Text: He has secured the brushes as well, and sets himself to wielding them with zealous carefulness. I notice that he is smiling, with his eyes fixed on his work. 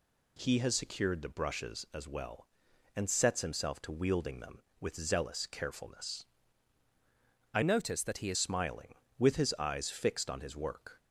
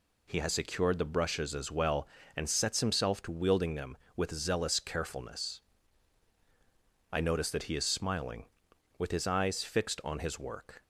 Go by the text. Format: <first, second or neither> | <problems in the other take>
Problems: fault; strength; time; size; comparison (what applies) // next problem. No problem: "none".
second | changes voice from "notice" to "is"; from 7.6 to 8.3 s; 0.7 s long